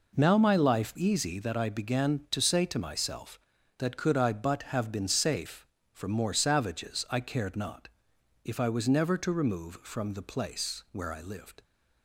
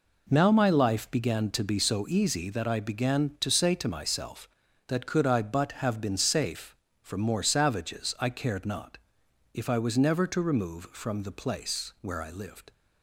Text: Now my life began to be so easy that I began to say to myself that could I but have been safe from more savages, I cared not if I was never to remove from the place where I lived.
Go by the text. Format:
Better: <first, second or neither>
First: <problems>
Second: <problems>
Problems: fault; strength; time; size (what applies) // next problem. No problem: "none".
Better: second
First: skips "began to be so"; at 0.9 s // pauses between "not" and "if"; noticeable; at 7.8 s; 0.56 s long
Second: pauses between "not" and "if"; noticeable; at 8.9 s; 0.56 s long